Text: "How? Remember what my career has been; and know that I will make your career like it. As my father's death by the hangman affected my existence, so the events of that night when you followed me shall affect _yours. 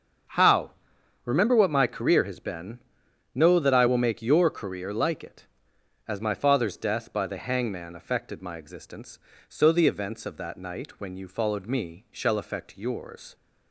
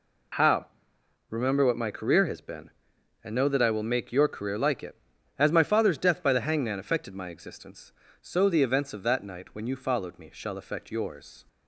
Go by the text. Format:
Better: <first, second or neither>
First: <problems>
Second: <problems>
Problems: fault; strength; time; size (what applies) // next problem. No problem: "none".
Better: second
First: starts louder than the rest; strong; until 1.8 s; 7 dB // skips "and"; at 3.0 s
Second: none